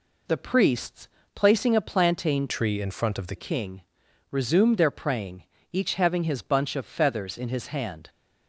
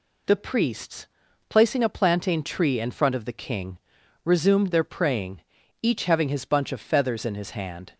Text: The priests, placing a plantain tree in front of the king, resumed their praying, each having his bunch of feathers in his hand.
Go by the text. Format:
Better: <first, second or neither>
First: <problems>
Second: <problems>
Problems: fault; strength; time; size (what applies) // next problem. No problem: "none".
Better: second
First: changes voice from "tree" to "the"; from 2.4 to 3.3 s; 0.9 s long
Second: none